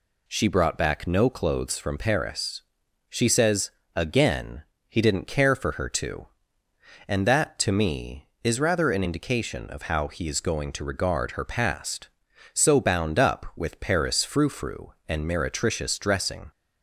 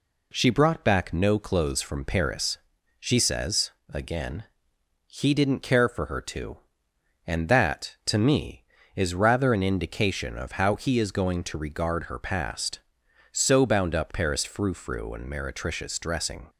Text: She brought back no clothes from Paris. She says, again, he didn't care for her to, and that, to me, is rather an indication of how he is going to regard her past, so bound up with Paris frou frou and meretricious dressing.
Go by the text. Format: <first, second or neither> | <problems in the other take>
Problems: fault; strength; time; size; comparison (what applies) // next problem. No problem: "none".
first | skips "with"; at 14.1 s